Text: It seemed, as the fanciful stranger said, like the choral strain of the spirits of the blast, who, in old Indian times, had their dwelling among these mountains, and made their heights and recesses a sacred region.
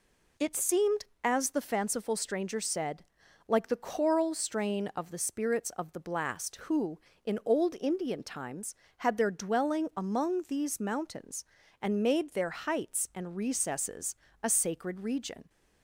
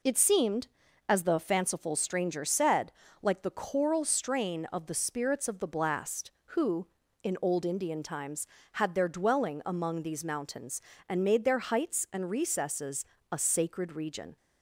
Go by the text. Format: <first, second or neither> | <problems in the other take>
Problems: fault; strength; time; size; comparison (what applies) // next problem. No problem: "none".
neither | pauses between "recesses" and "a"; slight; the same in both